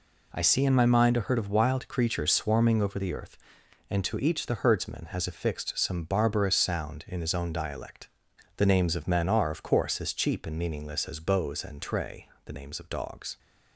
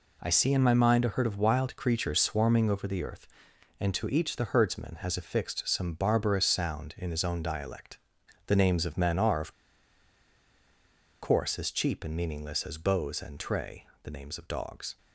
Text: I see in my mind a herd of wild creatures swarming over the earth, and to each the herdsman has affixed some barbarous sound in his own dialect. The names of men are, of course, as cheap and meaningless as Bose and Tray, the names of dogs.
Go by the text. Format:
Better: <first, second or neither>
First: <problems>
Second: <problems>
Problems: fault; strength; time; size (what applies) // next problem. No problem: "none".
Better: first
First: none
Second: pauses between "of" and "course"; strong; at 9.5 s; 1.6 s long